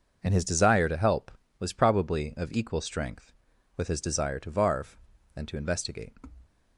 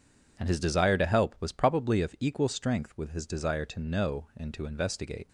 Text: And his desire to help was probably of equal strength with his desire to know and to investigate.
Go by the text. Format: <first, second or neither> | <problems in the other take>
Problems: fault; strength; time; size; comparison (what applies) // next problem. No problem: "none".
second | says "varve" for "know"; at 4.5 s